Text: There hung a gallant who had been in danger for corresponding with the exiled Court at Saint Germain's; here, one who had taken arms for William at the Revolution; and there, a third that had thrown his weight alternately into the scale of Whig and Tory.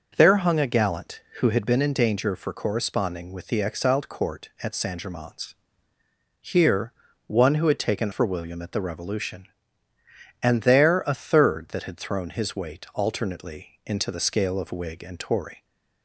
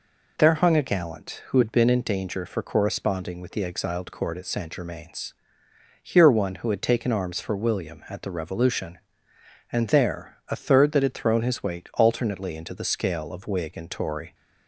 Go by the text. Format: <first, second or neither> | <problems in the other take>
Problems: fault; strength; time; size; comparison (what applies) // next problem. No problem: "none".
second | skips "arms"; at 8.1 s